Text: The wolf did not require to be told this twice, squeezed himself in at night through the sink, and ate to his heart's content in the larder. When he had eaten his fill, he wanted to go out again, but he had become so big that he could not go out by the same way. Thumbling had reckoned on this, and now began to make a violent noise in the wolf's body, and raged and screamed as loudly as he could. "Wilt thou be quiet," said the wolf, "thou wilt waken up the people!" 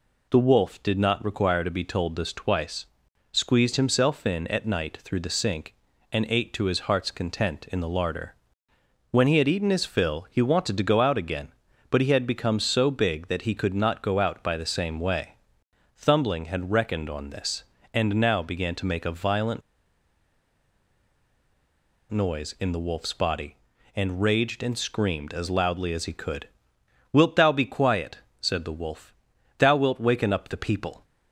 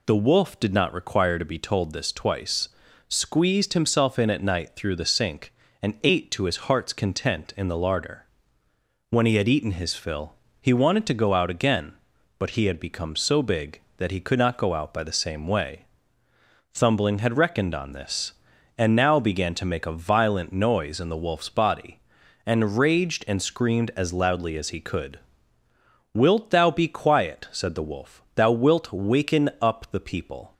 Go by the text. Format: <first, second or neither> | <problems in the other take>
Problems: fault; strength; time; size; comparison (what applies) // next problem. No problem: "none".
second | pauses between "violent" and "noise"; strong; at 19.6 s; 2.5 s long